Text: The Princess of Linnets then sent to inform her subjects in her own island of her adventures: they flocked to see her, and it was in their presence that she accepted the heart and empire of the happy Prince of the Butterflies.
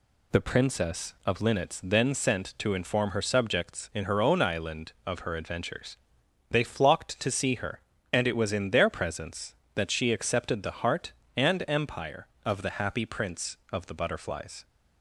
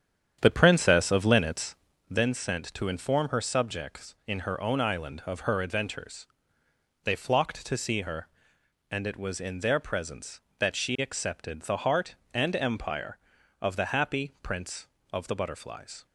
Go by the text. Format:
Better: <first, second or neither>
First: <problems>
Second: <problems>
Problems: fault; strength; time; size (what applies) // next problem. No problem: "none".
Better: first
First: none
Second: starts louder than the rest; strong; until 2.1 s; 9 dB // pauses between "Linnets" and "then"; slight; at 1.7 s; 0.34 s long